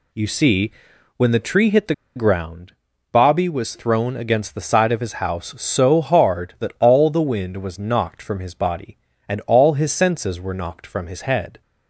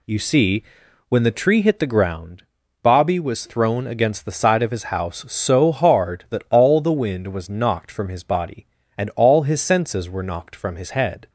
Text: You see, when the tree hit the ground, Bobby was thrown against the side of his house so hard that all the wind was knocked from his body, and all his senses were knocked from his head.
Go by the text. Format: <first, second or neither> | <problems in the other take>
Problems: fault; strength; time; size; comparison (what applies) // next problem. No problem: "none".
second | pauses between "the" and "ground"; slight; at 1.9 s; 0.22 s long